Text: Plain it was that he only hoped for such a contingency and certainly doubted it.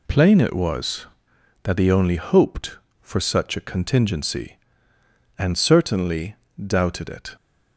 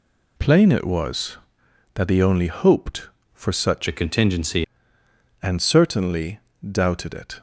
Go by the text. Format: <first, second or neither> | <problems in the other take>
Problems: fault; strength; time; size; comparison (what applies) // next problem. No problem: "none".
first | changes voice from "a" to "contingency"; from 3.8 to 4.6 s; 0.8 s long // pauses between "certainly" and "doubted"; slight; at 6.4 s; 0.32 s long; slight in the first